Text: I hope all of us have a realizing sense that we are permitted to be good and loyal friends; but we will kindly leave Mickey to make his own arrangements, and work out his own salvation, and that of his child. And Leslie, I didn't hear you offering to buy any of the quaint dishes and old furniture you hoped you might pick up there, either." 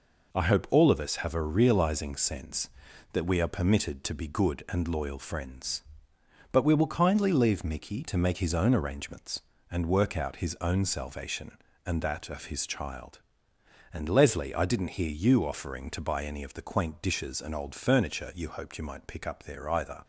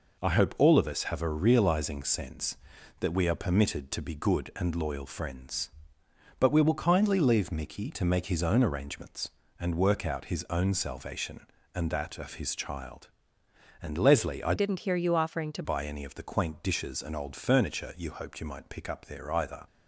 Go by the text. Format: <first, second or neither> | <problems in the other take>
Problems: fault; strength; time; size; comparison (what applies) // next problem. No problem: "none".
first | changes voice from "didn't" to "to"; from 14.5 to 15.6 s; 1.1 s long